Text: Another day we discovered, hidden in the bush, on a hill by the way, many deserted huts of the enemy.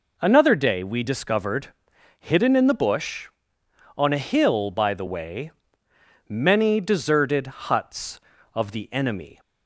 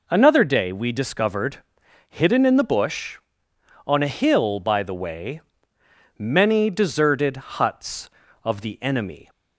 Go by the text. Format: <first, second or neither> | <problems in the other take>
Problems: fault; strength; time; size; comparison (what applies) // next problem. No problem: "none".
neither | none